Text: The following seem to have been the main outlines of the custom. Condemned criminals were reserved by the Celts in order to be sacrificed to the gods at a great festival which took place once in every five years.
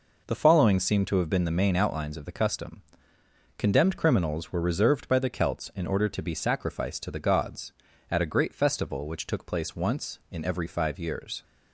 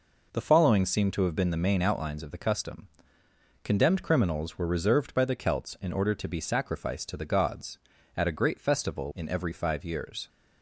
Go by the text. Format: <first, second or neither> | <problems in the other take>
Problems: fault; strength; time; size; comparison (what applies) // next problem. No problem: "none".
first | skips "which took place once"; at 9.1 s